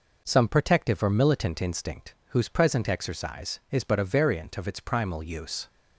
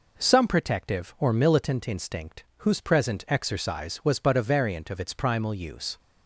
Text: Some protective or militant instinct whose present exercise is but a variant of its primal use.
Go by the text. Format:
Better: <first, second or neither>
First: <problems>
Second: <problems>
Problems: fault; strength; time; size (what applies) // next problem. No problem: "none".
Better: first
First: none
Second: says "was" for "is"; at 4.0 s